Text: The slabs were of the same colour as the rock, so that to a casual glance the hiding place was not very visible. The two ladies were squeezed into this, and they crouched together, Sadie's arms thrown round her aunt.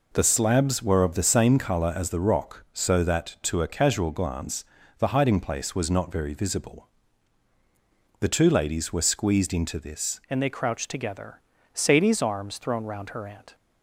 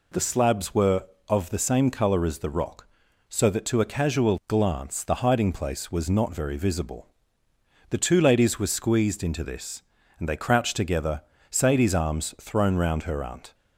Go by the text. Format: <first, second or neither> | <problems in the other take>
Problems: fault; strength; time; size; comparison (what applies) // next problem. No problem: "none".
second | pauses between "glance" and "the"; slight; at 4.6 s; 0.34 s long // changes voice at "and"; from 10.2 s on; 3.3 s long